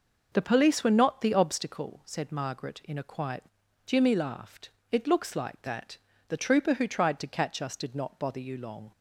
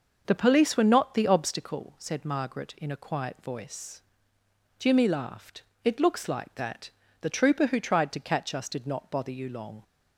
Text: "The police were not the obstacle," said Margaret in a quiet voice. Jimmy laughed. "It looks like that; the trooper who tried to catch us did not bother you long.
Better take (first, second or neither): second